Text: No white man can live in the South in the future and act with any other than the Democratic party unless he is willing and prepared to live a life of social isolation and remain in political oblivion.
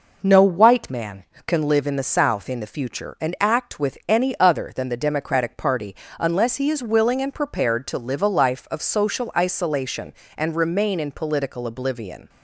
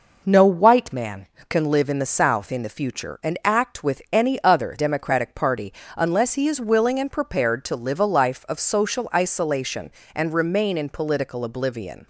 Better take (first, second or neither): first